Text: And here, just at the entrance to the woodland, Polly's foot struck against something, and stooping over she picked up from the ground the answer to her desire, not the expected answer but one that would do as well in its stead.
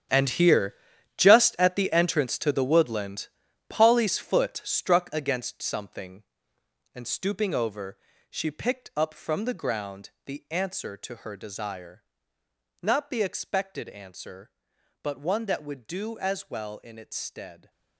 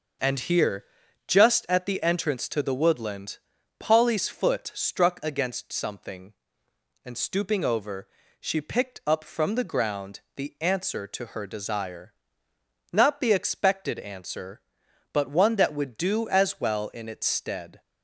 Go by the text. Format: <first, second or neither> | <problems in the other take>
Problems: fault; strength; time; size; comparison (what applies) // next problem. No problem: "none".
second | gets quieter; strong; throughout; 14 dB // starts louder than the rest; strong; until 1.5 s; 9 dB; noticeable in the second // pauses between "over" and "she"; slight; at 7.9 s; 0.36 s long; slight in the second // pauses between "ground" and "the"; slight; at 10.1 s; 0.16 s long; slight in the second